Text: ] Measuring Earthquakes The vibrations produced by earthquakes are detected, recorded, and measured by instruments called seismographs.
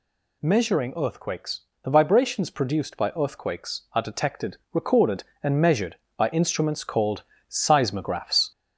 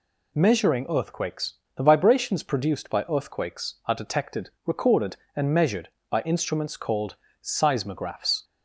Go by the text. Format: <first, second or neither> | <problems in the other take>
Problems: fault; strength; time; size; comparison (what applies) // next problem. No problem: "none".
second | gets louder; throughout; 4 dB // pauses between "Earthquakes" and "The"; slight; at 1.6 s; 0.18 s long; slight in the second // pauses between "called" and "seismographs"; slight; at 7.2 s; 0.26 s long; slight in the second